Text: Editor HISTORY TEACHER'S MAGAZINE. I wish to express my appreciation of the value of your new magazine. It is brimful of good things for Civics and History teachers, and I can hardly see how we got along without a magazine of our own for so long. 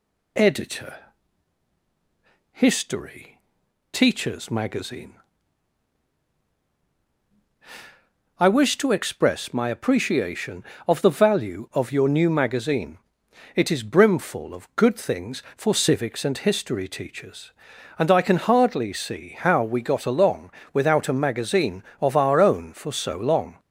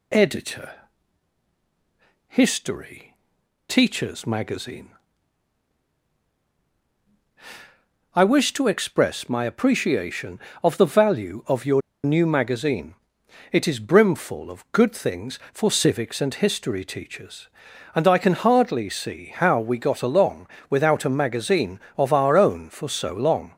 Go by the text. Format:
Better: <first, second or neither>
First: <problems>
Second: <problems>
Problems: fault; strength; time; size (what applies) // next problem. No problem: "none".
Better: first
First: pauses between "Editor" and "HISTORY"; strong; at 0.9 s; 1.5 s long // pauses between "HISTORY" and "TEACHER'S"; noticeable; at 3.4 s; 0.50 s long // pauses between "along" and "without"; slight; at 20.5 s; 0.20 s long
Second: pauses between "Editor" and "HISTORY"; strong; at 0.7 s; 1.5 s long // pauses between "HISTORY" and "TEACHER'S"; noticeable; at 3.1 s; 0.50 s long // pauses between "your" and "new"; slight; at 11.8 s; 0.23 s long // pauses between "along" and "without"; slight; at 20.4 s; 0.20 s long